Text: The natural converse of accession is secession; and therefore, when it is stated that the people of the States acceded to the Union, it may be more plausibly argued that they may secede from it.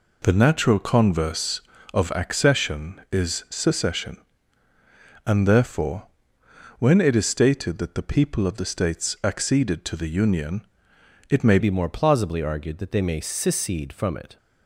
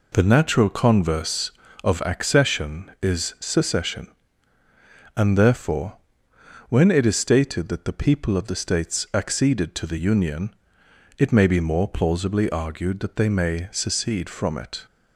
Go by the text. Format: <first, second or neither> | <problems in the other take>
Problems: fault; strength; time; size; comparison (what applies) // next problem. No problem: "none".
second | changes voice at "be"; from 11.5 s on; 2.8 s long